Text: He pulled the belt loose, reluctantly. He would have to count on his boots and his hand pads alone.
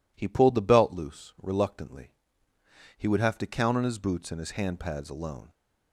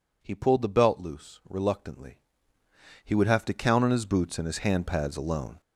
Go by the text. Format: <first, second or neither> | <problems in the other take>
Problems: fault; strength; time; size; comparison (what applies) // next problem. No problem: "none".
first | gets louder; throughout; 7 dB